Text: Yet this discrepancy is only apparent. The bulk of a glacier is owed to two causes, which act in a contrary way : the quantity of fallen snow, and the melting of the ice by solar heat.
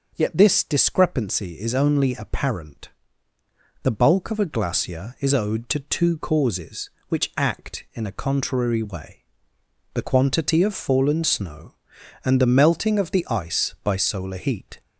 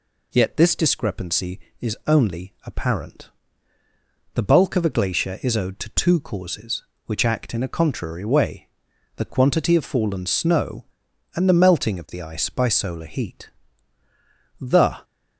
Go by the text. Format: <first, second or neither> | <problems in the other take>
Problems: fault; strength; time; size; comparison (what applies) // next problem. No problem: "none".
first | goes on to say "The"; slight; from 14.5 s on; 0.44 s long